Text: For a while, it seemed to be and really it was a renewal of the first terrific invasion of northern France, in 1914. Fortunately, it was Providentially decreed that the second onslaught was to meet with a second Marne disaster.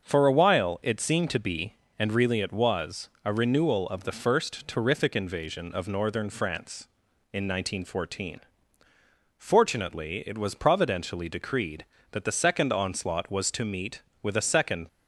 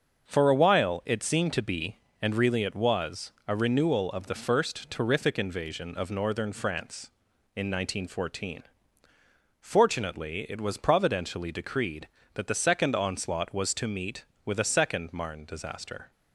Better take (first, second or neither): second